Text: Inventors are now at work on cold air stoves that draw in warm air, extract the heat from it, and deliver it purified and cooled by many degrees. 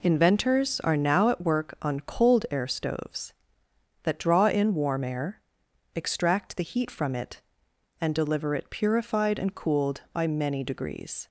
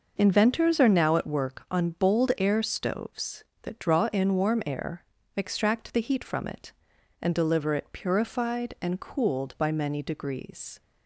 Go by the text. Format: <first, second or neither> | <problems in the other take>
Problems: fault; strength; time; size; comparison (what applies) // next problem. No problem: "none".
first | says "bold" for "cold"; at 1.8 s